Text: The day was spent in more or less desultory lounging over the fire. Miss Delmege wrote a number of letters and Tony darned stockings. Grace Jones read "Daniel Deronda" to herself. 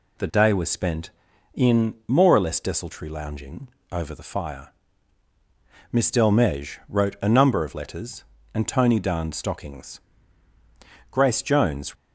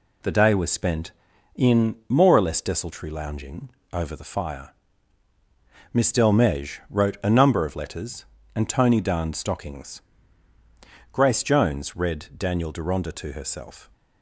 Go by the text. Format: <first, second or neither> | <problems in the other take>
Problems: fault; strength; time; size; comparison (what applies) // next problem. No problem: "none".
second | pauses between "lounging" and "over"; slight; at 3.6 s; 0.24 s long; slight in the second // stops before "read Daniel Deronda to herself"; at 11.9 s